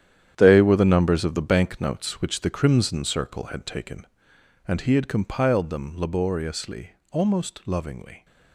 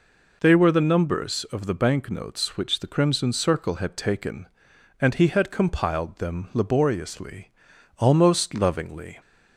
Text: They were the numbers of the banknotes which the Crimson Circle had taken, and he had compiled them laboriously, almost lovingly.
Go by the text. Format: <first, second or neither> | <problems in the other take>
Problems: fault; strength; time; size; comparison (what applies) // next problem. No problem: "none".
second | gets quieter; strong; throughout; 11 dB